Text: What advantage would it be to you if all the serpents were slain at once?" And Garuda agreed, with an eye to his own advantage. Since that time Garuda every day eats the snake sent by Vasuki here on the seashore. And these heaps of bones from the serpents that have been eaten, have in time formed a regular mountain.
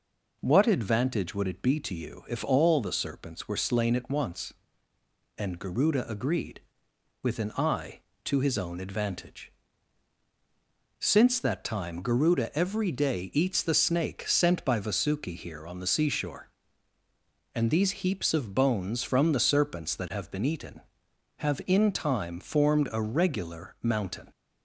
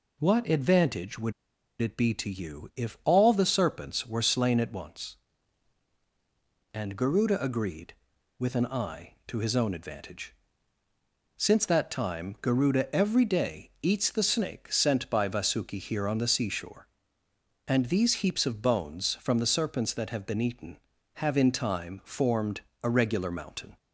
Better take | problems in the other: first | pauses between "would" and "it"; noticeable; at 1.3 s; 0.47 s long // pauses between "formed" and "a"; slight; at 22.6 s; 0.22 s long

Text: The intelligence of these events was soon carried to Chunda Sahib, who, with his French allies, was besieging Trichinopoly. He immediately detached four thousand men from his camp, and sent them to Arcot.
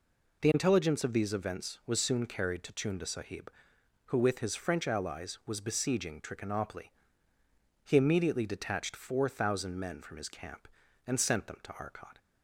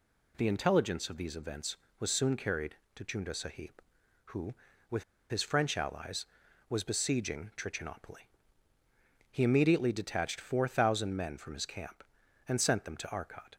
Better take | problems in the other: first | pauses between "with" and "his"; slight; at 5.0 s; 0.26 s long

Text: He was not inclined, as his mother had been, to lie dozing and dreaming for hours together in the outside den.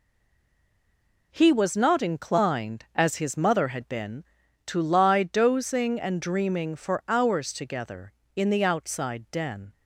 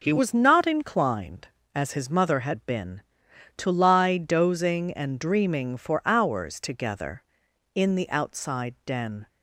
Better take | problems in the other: second | stays silent before the first word; noticeable; until 1.3 s; 1.3 s long

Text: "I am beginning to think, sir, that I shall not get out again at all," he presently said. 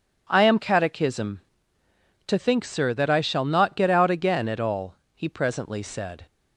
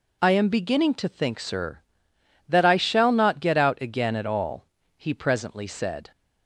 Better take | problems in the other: second | says "catechism" for "beginning"; at 0.5 s

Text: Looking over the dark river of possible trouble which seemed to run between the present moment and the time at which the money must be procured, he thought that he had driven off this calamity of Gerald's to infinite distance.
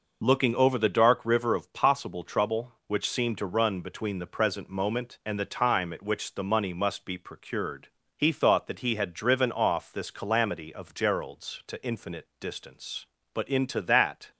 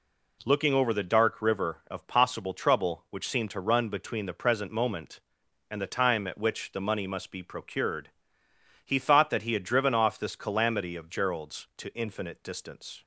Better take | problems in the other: second | goes on to say "But into that"; noticeable; from 13.3 s on; 0.96 s long

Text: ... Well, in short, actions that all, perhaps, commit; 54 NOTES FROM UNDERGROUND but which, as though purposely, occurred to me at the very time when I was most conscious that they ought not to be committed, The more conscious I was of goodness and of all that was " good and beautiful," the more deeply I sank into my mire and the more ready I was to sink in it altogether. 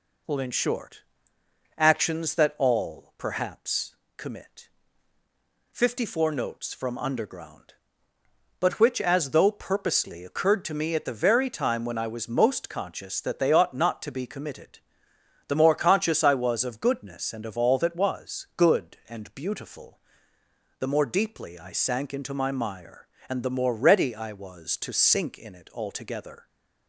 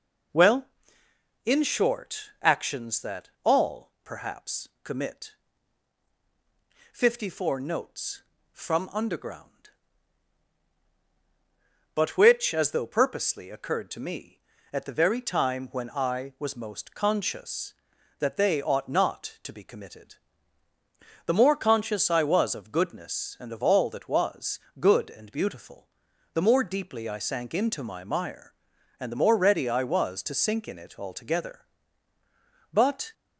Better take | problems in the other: first | goes on to say "But"; slight; from 32.7 s on; 0.40 s long

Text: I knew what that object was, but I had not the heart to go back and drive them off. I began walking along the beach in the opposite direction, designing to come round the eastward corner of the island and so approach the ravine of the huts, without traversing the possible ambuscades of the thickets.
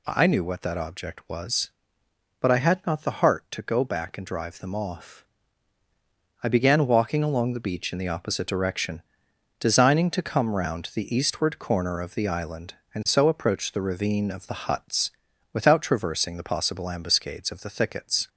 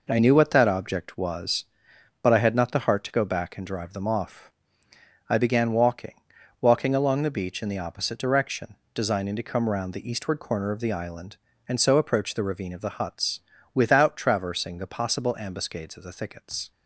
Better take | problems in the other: first | says "walking" twice; at 6.5 s

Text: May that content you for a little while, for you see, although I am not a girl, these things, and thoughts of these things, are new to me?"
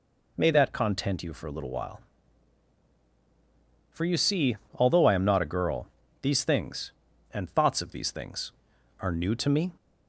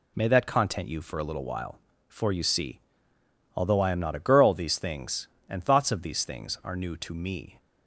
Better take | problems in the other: neither | none

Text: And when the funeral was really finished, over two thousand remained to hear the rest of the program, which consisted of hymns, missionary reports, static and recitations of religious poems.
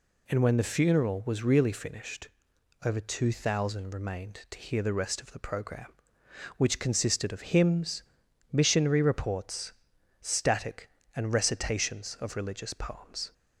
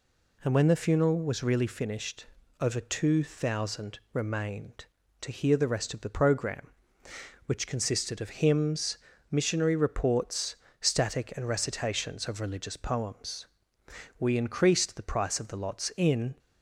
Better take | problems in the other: first | goes on to say "We increased the price of the lots in"; strong; from 14.1 s on; 2.1 s long

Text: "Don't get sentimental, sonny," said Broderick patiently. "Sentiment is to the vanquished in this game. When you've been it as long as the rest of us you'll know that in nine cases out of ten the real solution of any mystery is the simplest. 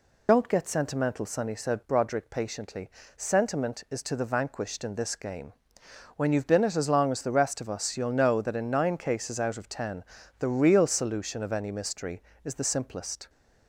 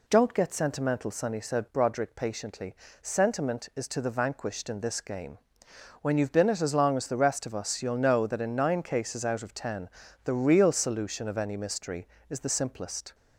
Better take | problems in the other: second | loses the start of "Don't"; at 0.2 s; 60 ms // pauses between "ten" and "the"; slight; at 10.0 s; 0.34 s long; slight in the second

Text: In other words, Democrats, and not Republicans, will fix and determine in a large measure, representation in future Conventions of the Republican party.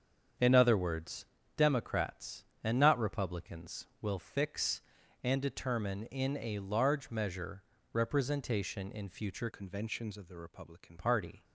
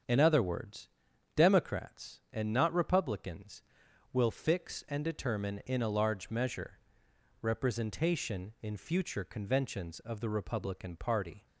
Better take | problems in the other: second | starts louder than the rest; strong; until 1.7 s; 7.5 dB; also in the second // changes voice from "Conventions" to "Republican"; from 9.5 to 10.9 s; 1.4 s long

